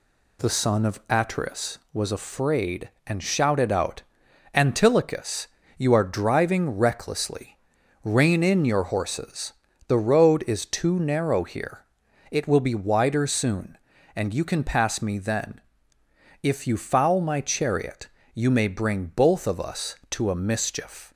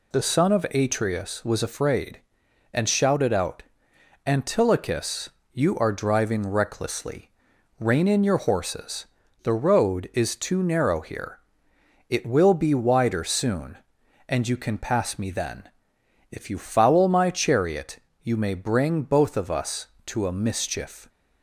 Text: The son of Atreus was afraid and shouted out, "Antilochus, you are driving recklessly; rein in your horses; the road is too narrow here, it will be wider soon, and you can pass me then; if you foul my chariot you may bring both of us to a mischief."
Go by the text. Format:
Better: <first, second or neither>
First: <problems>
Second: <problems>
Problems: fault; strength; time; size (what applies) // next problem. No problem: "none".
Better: neither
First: pauses between "chariot" and "you"; slight; at 18.0 s; 0.24 s long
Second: pauses between "chariot" and "you"; slight; at 17.9 s; 0.24 s long